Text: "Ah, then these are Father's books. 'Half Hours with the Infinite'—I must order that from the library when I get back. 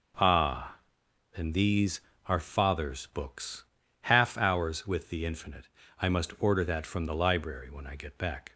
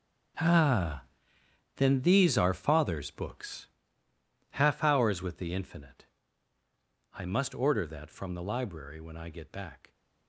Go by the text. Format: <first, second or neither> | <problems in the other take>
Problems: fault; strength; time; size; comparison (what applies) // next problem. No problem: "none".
first | gets quieter; strong; throughout; 14.5 dB